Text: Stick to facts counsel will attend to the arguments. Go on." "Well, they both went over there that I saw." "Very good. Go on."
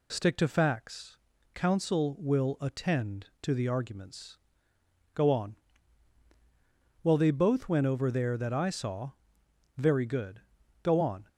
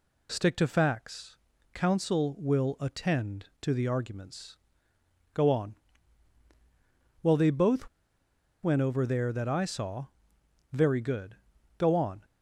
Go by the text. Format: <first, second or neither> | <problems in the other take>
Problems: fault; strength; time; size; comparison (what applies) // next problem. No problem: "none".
first | pauses between "facts" and "counsel"; at 1.3 s; 0.40 s long; also in the first // pauses between "both" and "went"; noticeable; at 7.8 s; 0.75 s long